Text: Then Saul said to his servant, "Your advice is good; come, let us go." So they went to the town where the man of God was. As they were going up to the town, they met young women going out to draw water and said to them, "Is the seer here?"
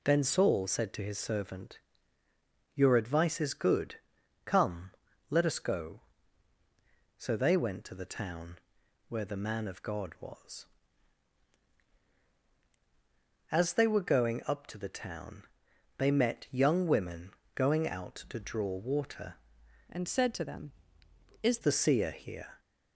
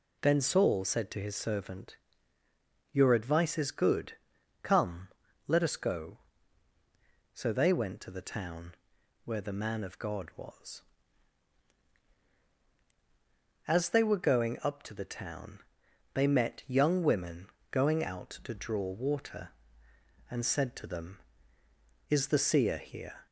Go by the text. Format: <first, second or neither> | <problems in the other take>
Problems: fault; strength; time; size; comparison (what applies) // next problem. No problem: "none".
second | pauses between "town" and "where"; noticeable; at 8.5 s; 0.52 s long; noticeable in the second // pauses between "women" and "going"; slight; at 17.3 s; 0.22 s long; slight in the second // changes voice from "and" to "Is"; from 19.9 to 21.5 s; 1.6 s long